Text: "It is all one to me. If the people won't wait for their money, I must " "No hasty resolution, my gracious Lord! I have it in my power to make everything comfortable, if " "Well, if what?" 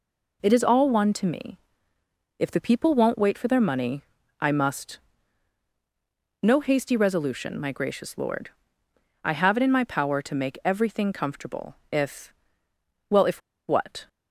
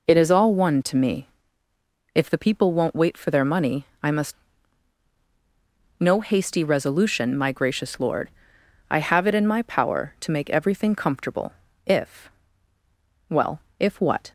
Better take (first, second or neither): second